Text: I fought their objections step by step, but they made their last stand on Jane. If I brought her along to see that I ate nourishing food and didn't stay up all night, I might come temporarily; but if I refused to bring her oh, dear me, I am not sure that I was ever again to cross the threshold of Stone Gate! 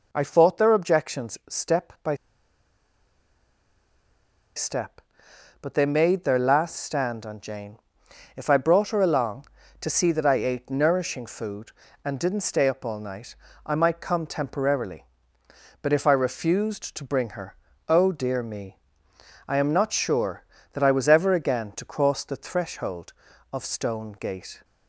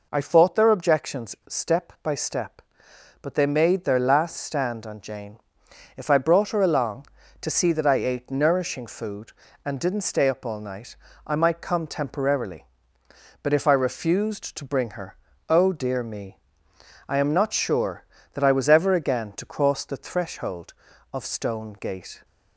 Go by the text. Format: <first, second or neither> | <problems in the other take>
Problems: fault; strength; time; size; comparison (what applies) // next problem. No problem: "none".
second | pauses between "by" and "step"; strong; at 2.1 s; 2.4 s long // pauses between "her" and "oh"; slight; at 17.5 s; 0.34 s long; slight in the second